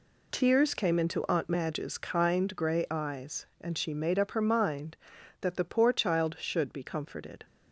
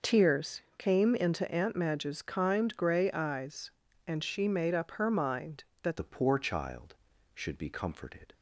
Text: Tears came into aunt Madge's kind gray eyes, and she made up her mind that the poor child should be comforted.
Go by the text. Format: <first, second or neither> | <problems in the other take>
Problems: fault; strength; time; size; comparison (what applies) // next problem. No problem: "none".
first | pauses between "Tears" and "came"; slight; at 0.6 s; 0.16 s long // changes voice at "the"; from 5.9 s on; 2.4 s long